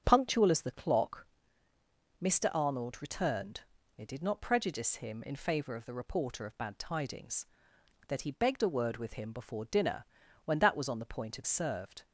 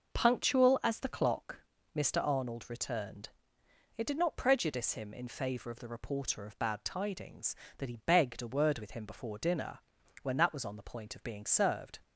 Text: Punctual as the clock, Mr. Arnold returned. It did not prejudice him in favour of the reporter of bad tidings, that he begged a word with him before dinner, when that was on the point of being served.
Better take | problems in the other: second | starts louder than the rest; strong; until 1.0 s; 8 dB // skips "being"; at 11.4 s

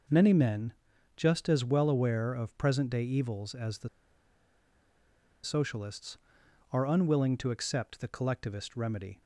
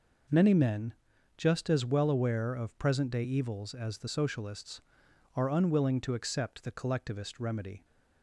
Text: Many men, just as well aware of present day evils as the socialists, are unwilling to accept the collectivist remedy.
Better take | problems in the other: second | pauses between "the" and "socialists"; strong; at 3.8 s; 1.5 s long

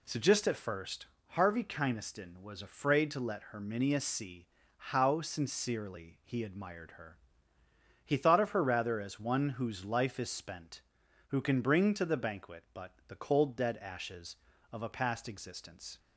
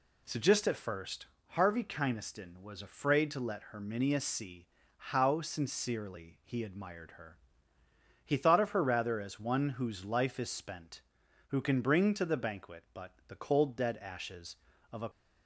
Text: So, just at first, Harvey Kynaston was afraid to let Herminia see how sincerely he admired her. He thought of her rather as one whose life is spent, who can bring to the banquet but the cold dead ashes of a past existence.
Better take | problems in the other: first | pauses between "see" and "how"; slight; at 4.6 s; 0.30 s long; slight in the first // stops before "past existence"; at 15.1 s

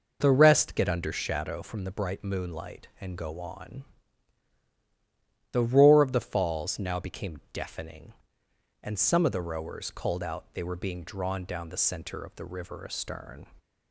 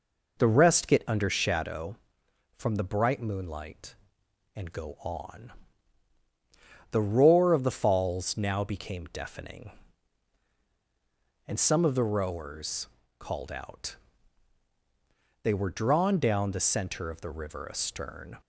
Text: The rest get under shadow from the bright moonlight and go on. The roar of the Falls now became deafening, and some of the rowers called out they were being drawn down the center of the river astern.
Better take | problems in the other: first | pauses between "rowers" and "called"; slight; at 12.8 s; 0.32 s long // pauses between "out" and "they"; strong; at 13.9 s; 1.4 s long // skips "being"; at 15.7 s

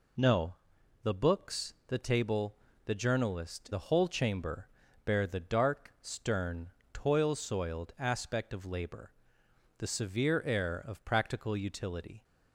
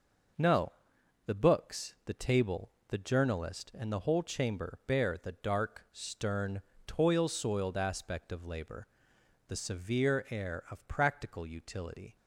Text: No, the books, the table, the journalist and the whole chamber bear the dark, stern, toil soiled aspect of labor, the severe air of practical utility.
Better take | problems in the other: second | skips "and"; at 3.7 s // pauses between "chamber" and "bear"; slight; at 4.6 s; 0.36 s long

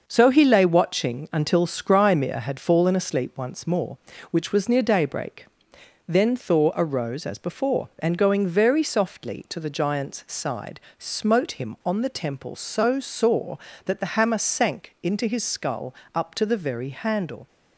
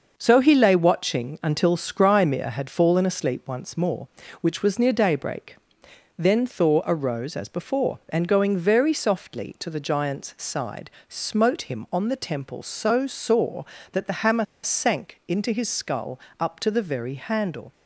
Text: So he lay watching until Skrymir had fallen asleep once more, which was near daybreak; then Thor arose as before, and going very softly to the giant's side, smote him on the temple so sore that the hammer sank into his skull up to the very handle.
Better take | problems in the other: first | pauses between "hammer" and "sank"; slight; at 14.4 s; 0.18 s long // pauses between "skull" and "up"; slight; at 16.1 s; 0.22 s long; slight in the first

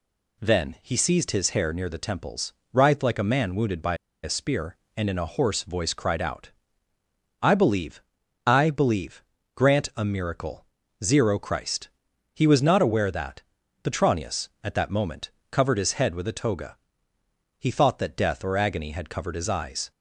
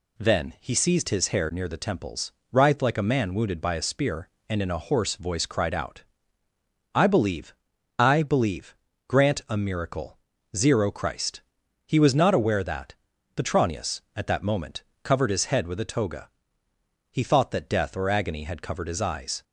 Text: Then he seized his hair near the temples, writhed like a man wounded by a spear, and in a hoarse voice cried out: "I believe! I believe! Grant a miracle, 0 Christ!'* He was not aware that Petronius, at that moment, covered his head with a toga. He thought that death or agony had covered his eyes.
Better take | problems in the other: second | pauses between "by" and "a"; slight; at 3.9 s; 0.27 s long // pauses between "that" and "Petronius"; at 13.4 s; 0.40 s long; also in the second

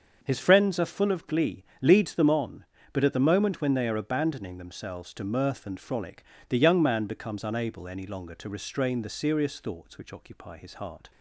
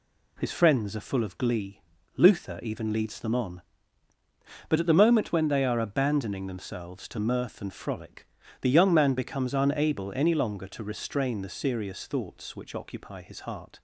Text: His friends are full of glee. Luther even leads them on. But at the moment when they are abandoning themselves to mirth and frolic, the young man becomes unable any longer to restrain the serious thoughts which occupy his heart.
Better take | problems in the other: second | starts louder than the rest; until 1.2 s; 6.5 dB // skips "Luther even"; at 1.7 s

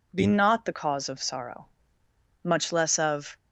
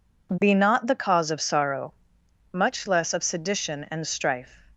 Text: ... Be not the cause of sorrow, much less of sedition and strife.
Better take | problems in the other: second | stops before "sedition and strife"; at 3.3 s

